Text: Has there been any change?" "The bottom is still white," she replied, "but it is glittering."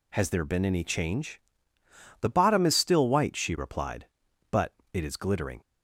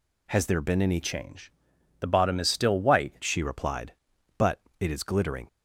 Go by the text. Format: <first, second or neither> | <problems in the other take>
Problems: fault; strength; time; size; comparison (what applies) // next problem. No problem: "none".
first | changes voice from "change" to "white"; from 1.0 to 3.1 s; 2.1 s long // pauses between "but" and "it"; slight; at 4.6 s; 0.18 s long; slight in the first